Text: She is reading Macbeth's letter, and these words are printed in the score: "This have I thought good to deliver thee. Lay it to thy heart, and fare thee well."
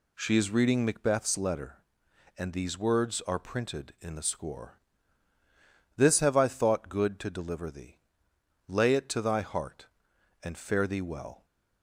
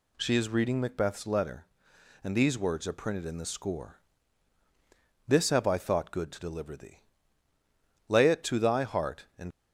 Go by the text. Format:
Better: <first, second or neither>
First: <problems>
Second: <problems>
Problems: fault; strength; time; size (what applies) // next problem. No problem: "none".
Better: first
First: none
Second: stops before "fare thee well"; at 9.5 s